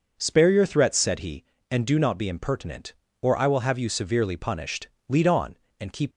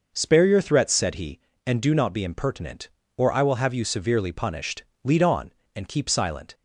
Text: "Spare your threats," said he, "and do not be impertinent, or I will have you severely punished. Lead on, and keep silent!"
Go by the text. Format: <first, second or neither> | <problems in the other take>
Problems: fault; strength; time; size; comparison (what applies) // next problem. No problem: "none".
second | starts louder than the rest; noticeable; until 1.1 s; 6 dB // stops before "silent"; at 6.1 s